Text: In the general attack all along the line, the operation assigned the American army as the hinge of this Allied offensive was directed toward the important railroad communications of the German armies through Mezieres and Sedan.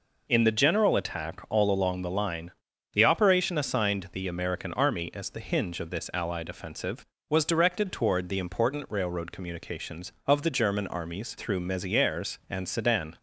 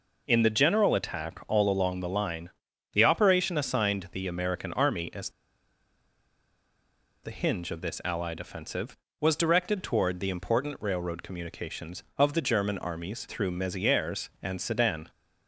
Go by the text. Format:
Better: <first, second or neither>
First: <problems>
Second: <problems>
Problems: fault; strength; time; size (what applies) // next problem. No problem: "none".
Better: first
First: none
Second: pauses between "as" and "the"; strong; at 5.2 s; 1.9 s long